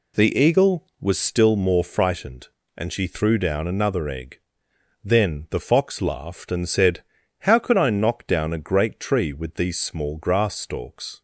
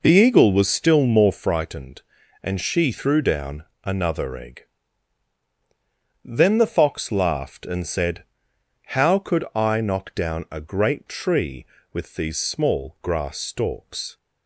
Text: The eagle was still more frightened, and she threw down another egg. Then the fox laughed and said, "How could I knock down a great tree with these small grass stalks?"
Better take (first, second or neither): first